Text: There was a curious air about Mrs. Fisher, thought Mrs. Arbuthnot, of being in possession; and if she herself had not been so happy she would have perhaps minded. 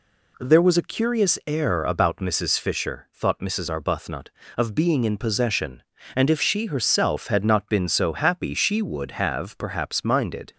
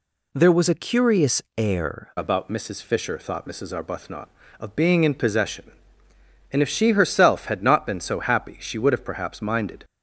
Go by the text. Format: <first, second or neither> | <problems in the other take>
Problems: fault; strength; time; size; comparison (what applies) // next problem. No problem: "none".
first | pauses between "curious" and "air"; slight; at 1.4 s; 0.16 s long // changes voice at "about"; from 2.1 s on; 7.7 s long